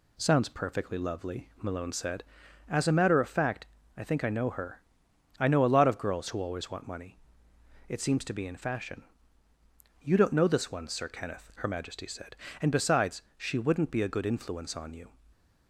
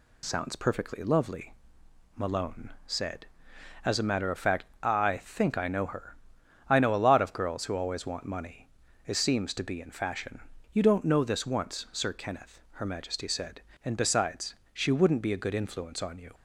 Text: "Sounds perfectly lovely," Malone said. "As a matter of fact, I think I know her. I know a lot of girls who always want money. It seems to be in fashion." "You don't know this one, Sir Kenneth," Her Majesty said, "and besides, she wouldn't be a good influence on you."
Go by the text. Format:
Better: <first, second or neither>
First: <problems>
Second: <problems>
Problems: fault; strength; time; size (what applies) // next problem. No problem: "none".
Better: first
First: none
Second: says "once" for "one"; at 11.4 s